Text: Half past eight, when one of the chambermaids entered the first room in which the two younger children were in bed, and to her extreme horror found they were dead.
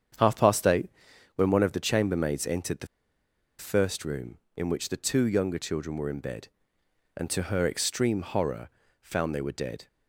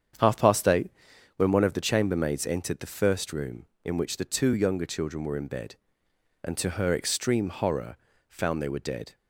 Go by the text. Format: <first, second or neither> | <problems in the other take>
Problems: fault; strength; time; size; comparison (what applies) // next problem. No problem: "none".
second | starts louder than the rest; strong; until 1.6 s; 8 dB; strong in the second // pauses between "the" and "first"; noticeable; at 2.8 s; 0.72 s long // pauses between "horror" and "found"; slight; at 8.6 s; 0.32 s long; slight in the second